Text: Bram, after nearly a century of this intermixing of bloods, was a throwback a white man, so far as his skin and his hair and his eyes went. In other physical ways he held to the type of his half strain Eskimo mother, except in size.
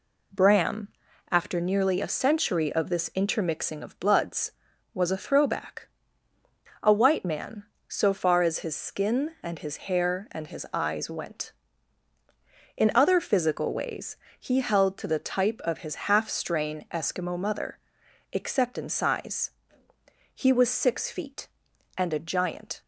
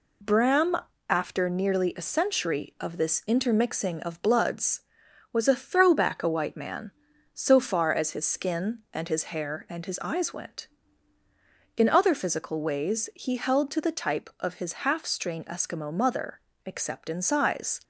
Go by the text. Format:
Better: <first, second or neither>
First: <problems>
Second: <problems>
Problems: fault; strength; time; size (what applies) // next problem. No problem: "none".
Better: second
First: pauses between "throwback" and "a"; noticeable; at 5.8 s; 0.96 s long // pauses between "ways" and "he"; slight; at 14.1 s; 0.24 s long // pauses between "his" and "half"; slight; at 15.9 s; 0.16 s long // goes on to say "He was six feet and a giant"; strong; from 20.3 s on; 2.4 s long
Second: none